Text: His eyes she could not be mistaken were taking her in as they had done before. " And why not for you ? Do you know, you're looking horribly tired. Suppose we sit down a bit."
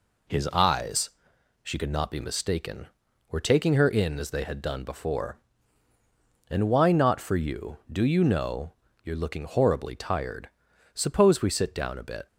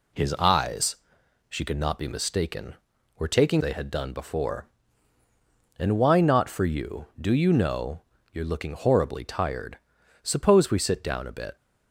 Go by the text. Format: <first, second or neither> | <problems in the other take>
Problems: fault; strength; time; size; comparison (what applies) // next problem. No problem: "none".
first | pauses between "eyes" and "she"; noticeable; at 0.9 s; 0.52 s long; noticeable in the first // skips "her in as"; at 3.6 s